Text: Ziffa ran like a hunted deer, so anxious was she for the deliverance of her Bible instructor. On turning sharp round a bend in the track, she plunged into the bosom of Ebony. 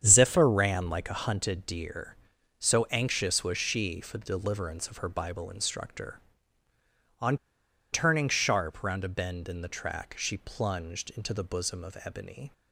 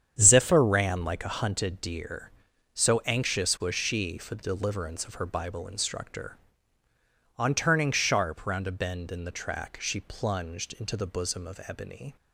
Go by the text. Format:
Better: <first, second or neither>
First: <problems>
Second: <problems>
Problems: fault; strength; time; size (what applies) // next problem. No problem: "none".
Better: second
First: starts louder than the rest; strong; until 1.0 s; 8.5 dB // pauses between "On" and "turning"; noticeable; at 7.3 s; 0.56 s long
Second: starts louder than the rest; strong; until 1.2 s; 8.5 dB